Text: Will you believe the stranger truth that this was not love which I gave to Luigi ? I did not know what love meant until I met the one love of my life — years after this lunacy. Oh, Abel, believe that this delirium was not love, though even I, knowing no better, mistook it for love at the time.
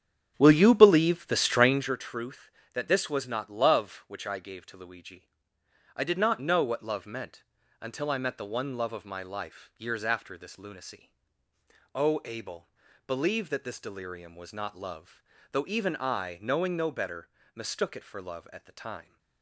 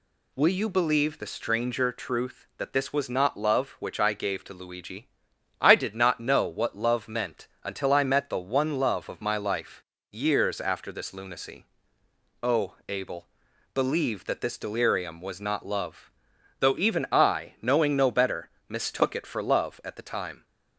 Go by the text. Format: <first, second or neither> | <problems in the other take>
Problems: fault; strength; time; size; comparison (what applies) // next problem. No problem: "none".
second | starts louder than the rest; strong; until 2.0 s; 8.5 dB // pauses between "meant" and "until"; slight; at 7.4 s; 0.36 s long